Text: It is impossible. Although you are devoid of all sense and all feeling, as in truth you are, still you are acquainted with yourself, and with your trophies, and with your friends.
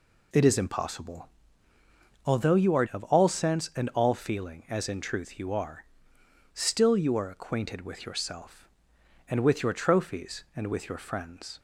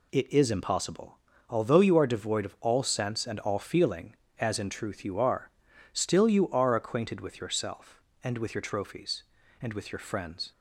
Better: second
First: skips "devoid"; at 2.8 s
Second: none

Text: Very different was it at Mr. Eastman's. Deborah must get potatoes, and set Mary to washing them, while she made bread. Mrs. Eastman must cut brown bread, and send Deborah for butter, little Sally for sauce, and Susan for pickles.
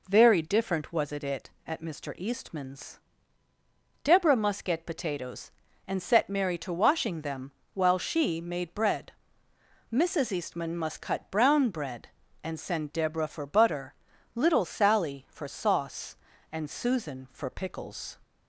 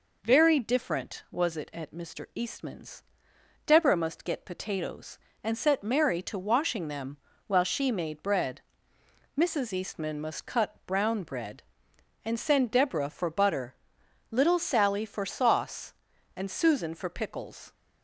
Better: second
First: says "it" twice; at 1.2 s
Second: none

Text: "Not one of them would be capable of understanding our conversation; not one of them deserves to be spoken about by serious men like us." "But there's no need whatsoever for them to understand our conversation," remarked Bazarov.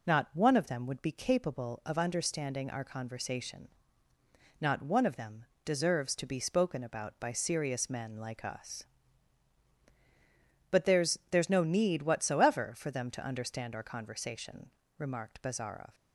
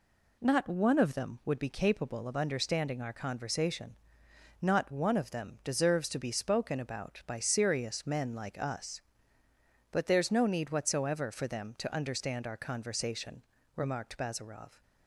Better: second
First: pauses between "them" and "deserves"; slight; at 5.4 s; 0.20 s long // says "there's" twice; at 11.3 s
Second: none

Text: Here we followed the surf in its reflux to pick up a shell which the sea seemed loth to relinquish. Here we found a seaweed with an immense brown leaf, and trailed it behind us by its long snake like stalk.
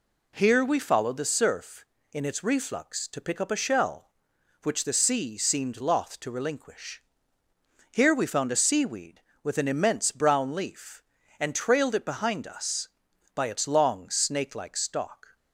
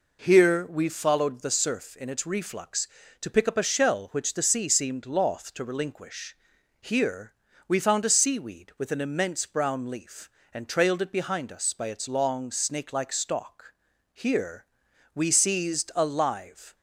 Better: first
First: none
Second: pauses between "Here" and "we"; slight; at 7.3 s; 0.36 s long // goes on to say "Here we seized a live"; strong; from 14.1 s on; 2.6 s long

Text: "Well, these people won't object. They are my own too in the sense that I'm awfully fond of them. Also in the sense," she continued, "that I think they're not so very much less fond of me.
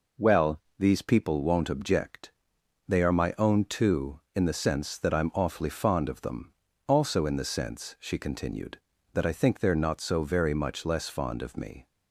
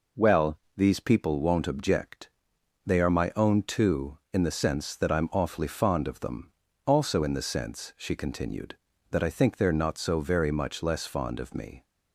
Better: neither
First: none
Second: none

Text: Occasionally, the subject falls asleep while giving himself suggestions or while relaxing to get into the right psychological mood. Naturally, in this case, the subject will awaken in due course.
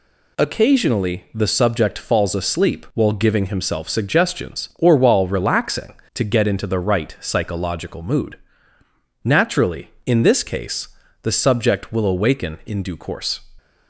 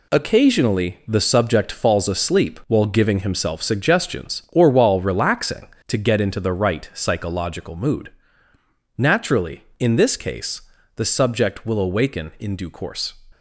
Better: first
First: none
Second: gets quieter; strong; throughout; 8 dB

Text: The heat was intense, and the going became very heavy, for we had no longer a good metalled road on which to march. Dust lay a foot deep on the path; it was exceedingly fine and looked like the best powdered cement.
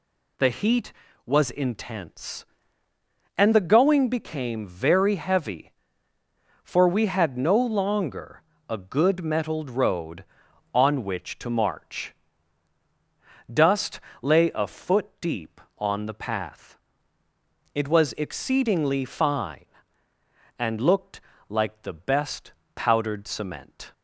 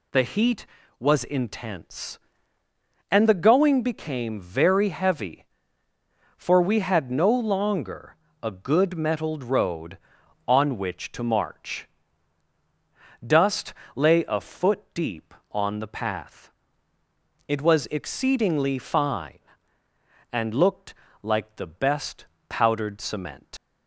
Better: first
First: pauses between "longer" and "a"; slight; at 8.4 s; 0.26 s long // pauses between "Dust" and "lay"; slight; at 14.0 s; 0.22 s long // pauses between "looked" and "like"; slight; at 21.2 s; 0.28 s long // pauses between "best" and "powdered"; slight; at 22.5 s; 0.24 s long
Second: pauses between "longer" and "a"; slight; at 8.1 s; 0.26 s long // pauses between "Dust" and "lay"; slight; at 13.7 s; 0.22 s long // pauses between "looked" and "like"; slight; at 20.9 s; 0.28 s long // pauses between "best" and "powdered"; slight; at 22.2 s; 0.24 s long // leaves "cement" unfinished; at 23.5 s; 90 ms

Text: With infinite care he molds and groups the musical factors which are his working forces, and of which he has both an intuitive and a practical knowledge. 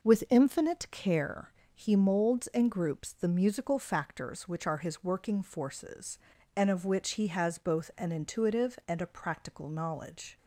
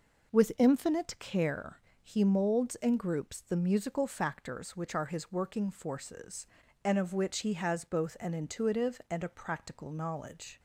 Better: neither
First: pauses between "care" and "he"; slight; at 1.5 s; 0.24 s long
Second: pauses between "care" and "he"; slight; at 1.7 s; 0.24 s long

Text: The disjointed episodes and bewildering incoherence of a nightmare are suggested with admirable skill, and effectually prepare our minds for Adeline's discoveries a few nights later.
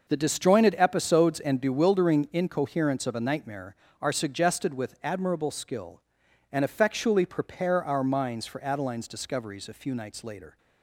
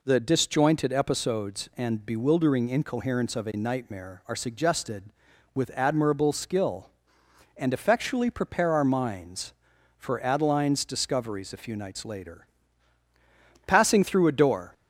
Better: first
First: none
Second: goes on to say "Passing through a door"; noticeable; from 13.6 s on; 1.0 s long

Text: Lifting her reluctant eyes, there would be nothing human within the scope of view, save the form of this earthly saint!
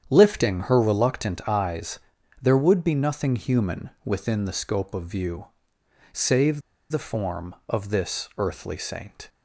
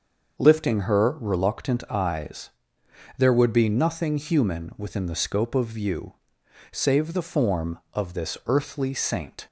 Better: second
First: starts louder than the rest; strong; until 1.1 s; 8.5 dB // pauses between "save" and "the"; slight; at 6.6 s; 0.29 s long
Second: starts louder than the rest; until 1.4 s; 6 dB

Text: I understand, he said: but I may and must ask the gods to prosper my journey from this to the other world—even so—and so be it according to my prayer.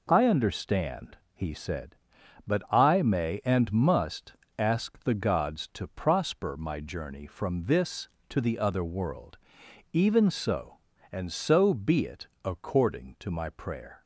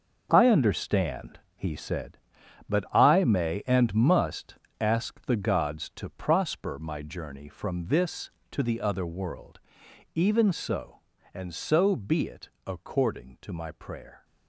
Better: first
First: pauses between "must" and "ask"; slight; at 4.3 s; 0.24 s long // pauses between "it" and "according"; slight; at 12.2 s; 0.16 s long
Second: gets quieter; strong; throughout; 10.5 dB // pauses between "must" and "ask"; slight; at 4.5 s; 0.24 s long // pauses between "it" and "according"; slight; at 12.4 s; 0.16 s long

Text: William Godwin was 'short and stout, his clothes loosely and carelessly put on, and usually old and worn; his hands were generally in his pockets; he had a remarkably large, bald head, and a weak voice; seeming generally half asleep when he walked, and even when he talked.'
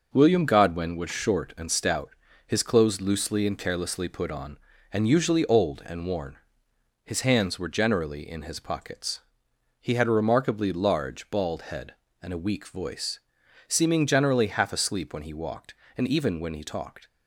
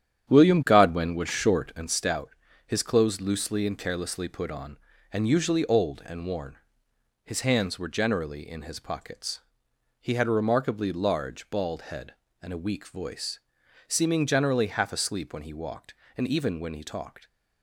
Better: first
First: none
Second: starts louder than the rest; strong; until 2.0 s; 9.5 dB

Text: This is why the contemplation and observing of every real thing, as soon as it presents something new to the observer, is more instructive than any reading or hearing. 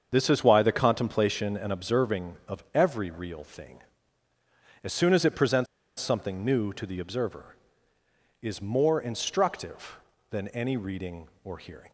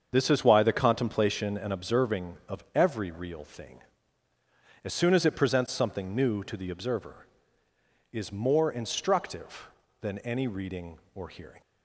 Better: second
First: starts louder than the rest; until 1.1 s; 7 dB // pauses between "presents" and "something"; slight; at 5.6 s; 0.33 s long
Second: starts louder than the rest; until 1.1 s; 7 dB

